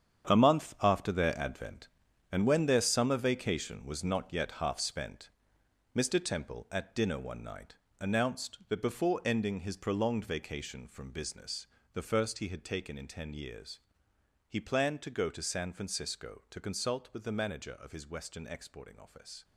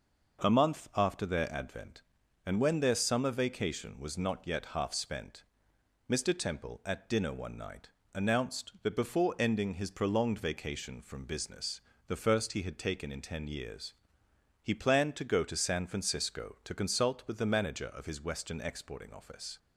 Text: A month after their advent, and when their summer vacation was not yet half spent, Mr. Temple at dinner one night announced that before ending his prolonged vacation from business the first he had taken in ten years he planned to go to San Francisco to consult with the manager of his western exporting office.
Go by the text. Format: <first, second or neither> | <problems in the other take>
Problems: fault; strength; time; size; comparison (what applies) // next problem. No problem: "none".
second | gets quieter; strong; throughout; 11 dB // pauses between "night" and "announced"; slight; at 7.7 s; 0.24 s long; slight in the second // pauses between "business" and "the"; slight; at 11.6 s; 0.26 s long; slight in the second // pauses between "years" and "he"; noticeable; at 13.7 s; 0.72 s long; noticeable in the second